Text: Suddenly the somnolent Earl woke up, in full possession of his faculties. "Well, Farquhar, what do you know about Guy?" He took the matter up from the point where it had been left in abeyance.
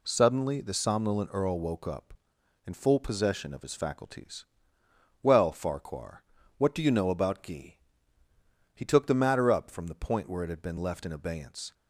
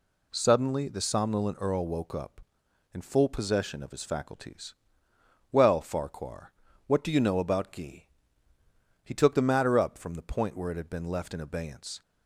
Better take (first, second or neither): neither